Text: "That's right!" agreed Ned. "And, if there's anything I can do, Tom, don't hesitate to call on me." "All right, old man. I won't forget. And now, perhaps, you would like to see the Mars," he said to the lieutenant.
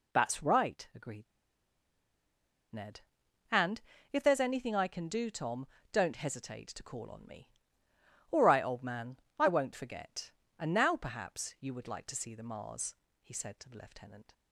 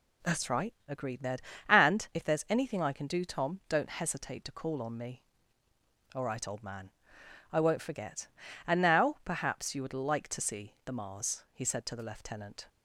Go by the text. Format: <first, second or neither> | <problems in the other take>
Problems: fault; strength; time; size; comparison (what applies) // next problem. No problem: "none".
second | pauses between "agreed" and "Ned"; strong; at 1.2 s; 1.4 s long